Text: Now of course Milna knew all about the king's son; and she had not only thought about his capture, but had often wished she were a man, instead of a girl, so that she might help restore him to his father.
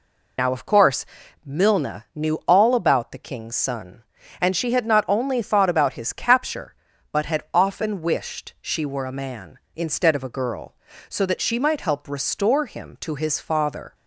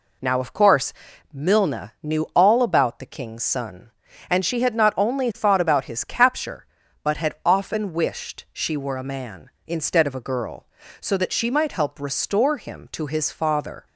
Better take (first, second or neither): second